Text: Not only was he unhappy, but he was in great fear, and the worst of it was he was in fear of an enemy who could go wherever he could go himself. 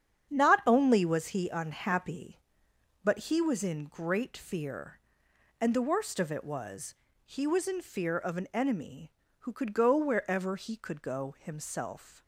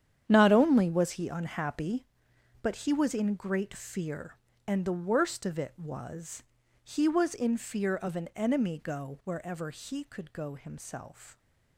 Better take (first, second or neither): first